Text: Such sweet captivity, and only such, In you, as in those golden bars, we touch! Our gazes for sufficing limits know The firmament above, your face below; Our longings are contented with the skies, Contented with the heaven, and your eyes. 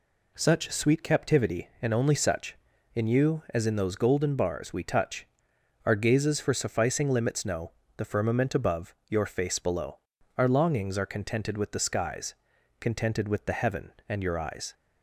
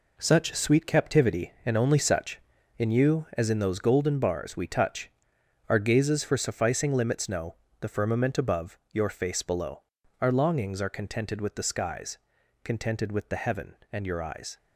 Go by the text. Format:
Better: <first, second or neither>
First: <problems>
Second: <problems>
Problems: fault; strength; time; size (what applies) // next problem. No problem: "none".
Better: first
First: pauses between "know" and "The"; slight; at 7.7 s; 0.26 s long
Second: gets quieter; strong; throughout; 8 dB // pauses between "know" and "The"; slight; at 7.5 s; 0.26 s long